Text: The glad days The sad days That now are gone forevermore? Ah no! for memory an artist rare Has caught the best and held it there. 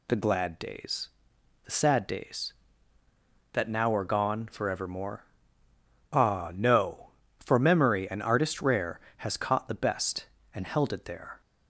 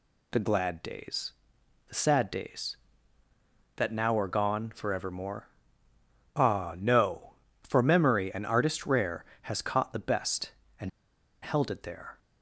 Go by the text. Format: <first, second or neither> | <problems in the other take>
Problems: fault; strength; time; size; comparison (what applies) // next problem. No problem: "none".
first | pauses between "days" and "The"; noticeable; at 1.3 s; 0.56 s long; noticeable in the first // pauses between "and" and "held"; noticeable; at 10.8 s; 0.54 s long